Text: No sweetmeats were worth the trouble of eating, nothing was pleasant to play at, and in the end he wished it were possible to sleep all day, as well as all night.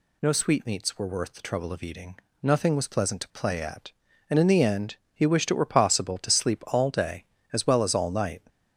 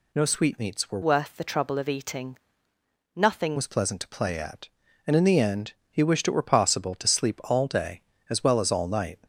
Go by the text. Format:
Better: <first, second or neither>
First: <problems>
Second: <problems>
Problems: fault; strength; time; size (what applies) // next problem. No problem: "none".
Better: first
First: pauses between "end" and "he"; slight; at 4.9 s; 0.18 s long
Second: changes voice from "worth" to "nothing"; from 1.0 to 3.5 s; 2.5 s long // pauses between "end" and "he"; slight; at 5.7 s; 0.18 s long